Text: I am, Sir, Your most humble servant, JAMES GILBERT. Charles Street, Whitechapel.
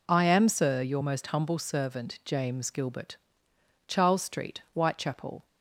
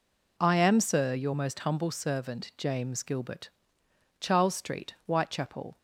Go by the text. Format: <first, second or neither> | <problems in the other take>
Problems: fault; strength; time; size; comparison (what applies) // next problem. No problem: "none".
neither | none